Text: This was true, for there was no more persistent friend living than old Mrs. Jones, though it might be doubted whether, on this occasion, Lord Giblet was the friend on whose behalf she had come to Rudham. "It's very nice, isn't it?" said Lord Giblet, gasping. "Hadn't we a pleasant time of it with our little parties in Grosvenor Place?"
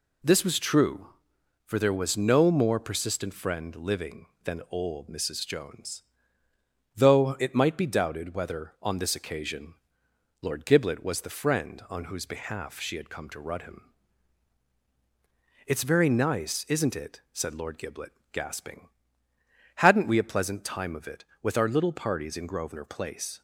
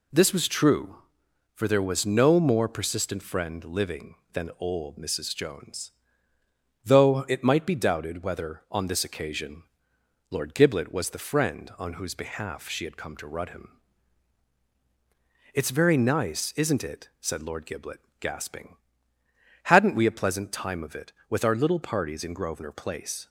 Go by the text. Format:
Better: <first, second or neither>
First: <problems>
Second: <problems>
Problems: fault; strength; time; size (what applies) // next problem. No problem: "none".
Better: neither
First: none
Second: none